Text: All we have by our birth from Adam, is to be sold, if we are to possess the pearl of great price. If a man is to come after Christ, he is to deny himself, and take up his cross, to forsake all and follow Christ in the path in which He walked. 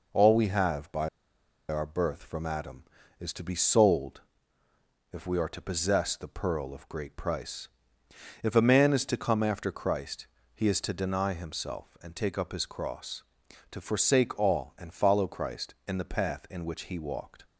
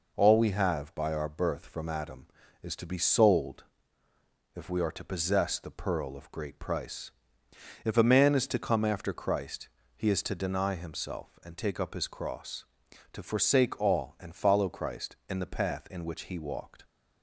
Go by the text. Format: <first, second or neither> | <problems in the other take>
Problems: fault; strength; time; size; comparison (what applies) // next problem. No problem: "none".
second | pauses between "by" and "our"; noticeable; at 1.0 s; 0.61 s long